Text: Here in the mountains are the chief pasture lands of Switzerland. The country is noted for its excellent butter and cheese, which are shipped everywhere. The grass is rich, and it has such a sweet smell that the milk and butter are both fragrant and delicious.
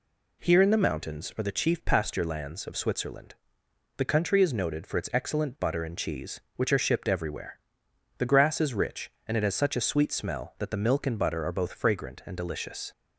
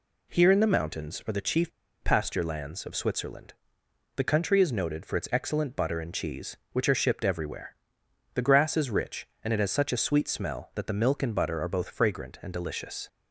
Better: first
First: none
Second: pauses between "chief" and "pasture"; slight; at 1.7 s; 0.31 s long

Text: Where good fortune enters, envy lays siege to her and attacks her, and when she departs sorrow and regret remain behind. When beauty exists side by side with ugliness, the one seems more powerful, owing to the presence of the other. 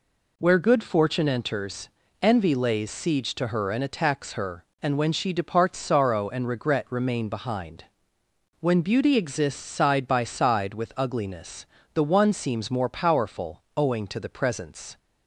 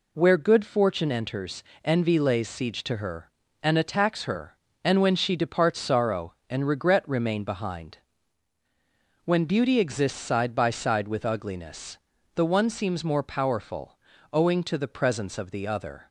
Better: second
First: stops before "of the other"; at 14.9 s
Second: none

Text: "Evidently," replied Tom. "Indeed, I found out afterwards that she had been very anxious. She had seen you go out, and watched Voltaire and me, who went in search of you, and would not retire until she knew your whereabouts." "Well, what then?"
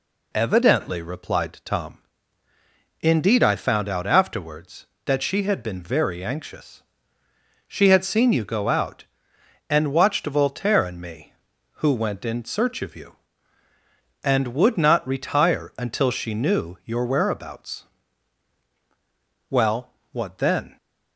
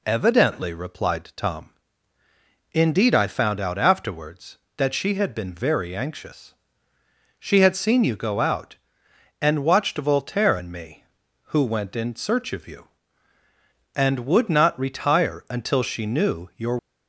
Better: first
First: none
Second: stops before "whereabouts Well what then"; at 16.7 s

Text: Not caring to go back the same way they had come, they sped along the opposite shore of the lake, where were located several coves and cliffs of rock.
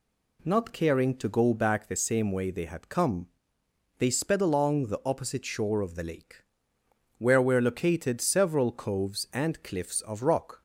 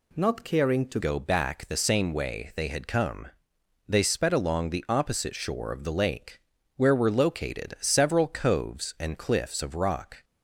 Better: first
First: none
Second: changes voice at "go"; from 1.0 s on; 9.2 s long

